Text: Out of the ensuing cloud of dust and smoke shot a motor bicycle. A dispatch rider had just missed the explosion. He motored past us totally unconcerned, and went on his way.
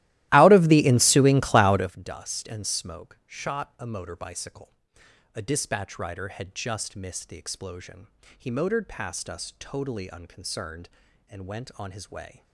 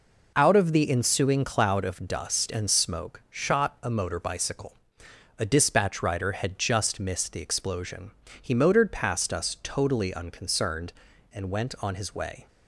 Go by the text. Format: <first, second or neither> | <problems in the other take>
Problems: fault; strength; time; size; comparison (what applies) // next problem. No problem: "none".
second | starts louder than the rest; strong; until 1.9 s; 16 dB